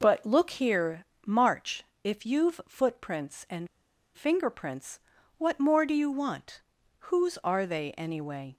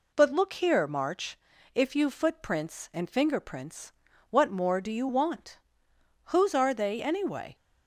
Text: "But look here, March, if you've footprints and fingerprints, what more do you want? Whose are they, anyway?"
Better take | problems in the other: second | pauses between "and" and "fingerprints"; noticeable; at 3.6 s; 0.49 s long

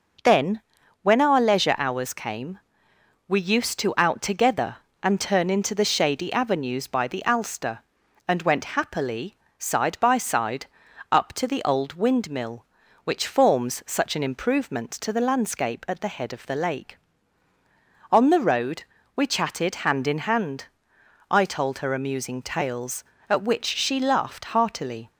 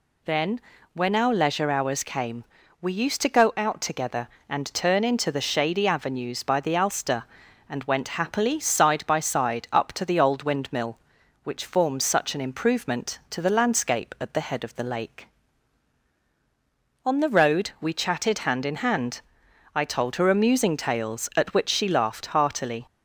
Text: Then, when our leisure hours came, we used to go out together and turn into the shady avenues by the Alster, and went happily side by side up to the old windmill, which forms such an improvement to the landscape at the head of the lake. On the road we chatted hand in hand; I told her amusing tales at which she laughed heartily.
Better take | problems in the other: second | skips "go"; at 3.9 s // pauses between "happily" and "side"; slight; at 9.3 s; 0.22 s long // pauses between "side" and "up"; at 10.6 s; 0.44 s long // pauses between "road" and "we"; slight; at 18.8 s; 0.32 s long

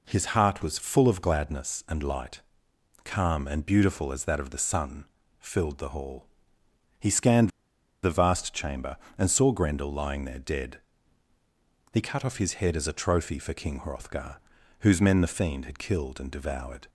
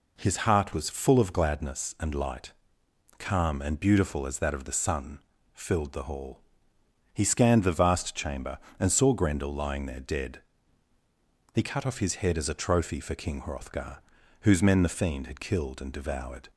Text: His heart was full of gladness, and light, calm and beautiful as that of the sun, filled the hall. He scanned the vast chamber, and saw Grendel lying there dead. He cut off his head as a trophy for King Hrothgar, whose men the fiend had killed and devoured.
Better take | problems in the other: second | pauses between "scanned" and "the"; noticeable; at 7.4 s; 0.53 s long

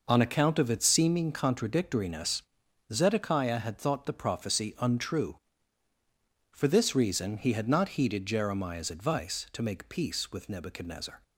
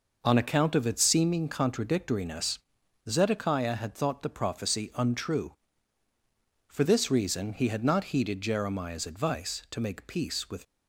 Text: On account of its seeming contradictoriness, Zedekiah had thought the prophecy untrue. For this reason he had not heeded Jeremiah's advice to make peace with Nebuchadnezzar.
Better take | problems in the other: first | stops before "Nebuchadnezzar"; at 10.6 s

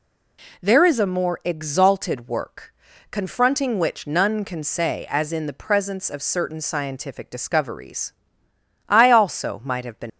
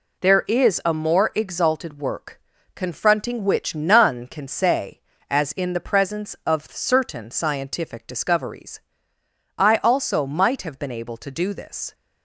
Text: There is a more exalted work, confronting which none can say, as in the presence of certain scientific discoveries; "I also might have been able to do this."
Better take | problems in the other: second | stops before "able to do this"; at 10.0 s

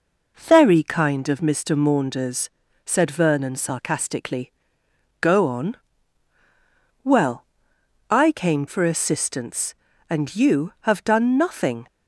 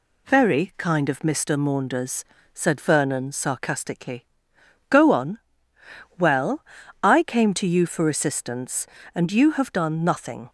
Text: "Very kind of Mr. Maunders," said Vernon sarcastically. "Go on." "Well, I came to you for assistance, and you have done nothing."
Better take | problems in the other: second | skips "to you"; at 8.6 s

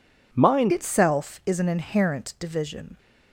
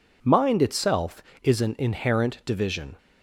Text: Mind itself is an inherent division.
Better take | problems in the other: second | changes voice at "itself"; from 0.7 s on; 2.2 s long

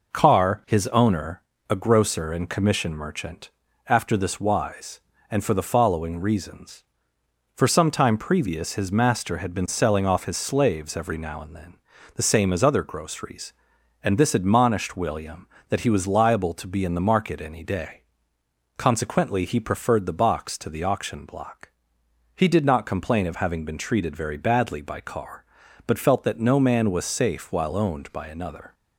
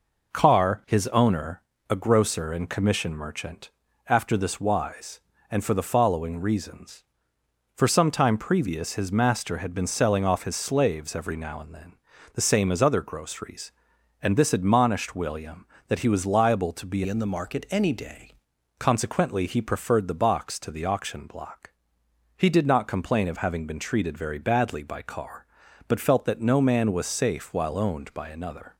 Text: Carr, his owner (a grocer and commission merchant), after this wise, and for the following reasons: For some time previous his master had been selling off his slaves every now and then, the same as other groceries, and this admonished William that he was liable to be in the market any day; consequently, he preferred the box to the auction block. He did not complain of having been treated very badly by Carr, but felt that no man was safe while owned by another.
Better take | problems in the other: first | changes voice from "in" to "day"; from 17.0 to 18.3 s; 1.3 s long

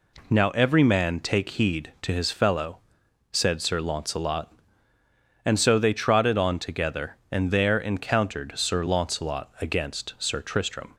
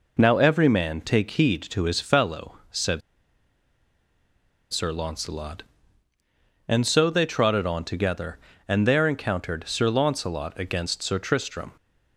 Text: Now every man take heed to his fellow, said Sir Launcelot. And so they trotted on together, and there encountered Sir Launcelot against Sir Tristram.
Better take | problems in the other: first | pauses between "said" and "Sir"; strong; at 3.0 s; 1.7 s long

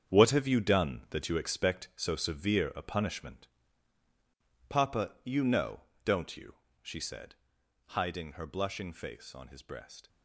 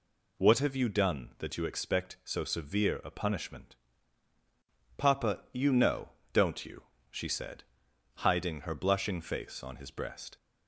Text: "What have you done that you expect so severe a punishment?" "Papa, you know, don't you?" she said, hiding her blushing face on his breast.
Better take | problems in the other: second | gets quieter; strong; throughout; 10.5 dB

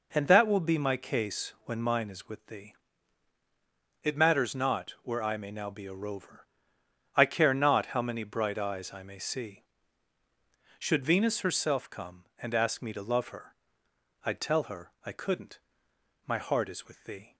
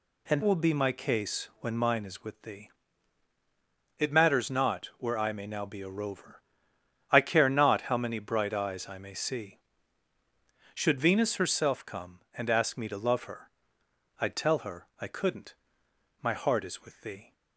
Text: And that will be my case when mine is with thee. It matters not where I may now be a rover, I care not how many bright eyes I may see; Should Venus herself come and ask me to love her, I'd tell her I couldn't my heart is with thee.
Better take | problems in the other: first | skips "that"; at 0.4 s // pauses between "couldn't" and "my"; noticeable; at 15.5 s; 0.68 s long; noticeable in the first

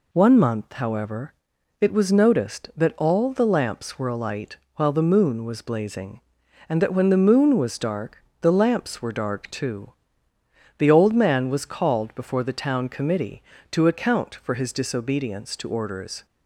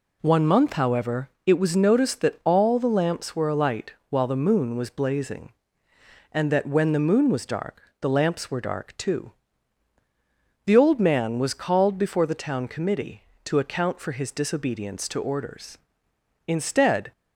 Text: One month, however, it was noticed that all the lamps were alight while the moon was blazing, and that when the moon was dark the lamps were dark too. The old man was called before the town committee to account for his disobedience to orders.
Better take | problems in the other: first | pauses between "alight" and "while"; slight; at 3.9 s; 0.16 s long; slight in the first // pauses between "dark" and "the"; slight; at 7.8 s; 0.20 s long; slight in the first // goes on to say "Instead"; noticeable; from 16.4 s on; 0.64 s long

